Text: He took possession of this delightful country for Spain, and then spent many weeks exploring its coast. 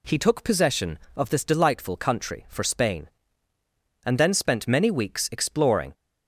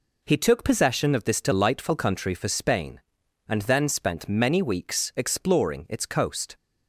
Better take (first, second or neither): second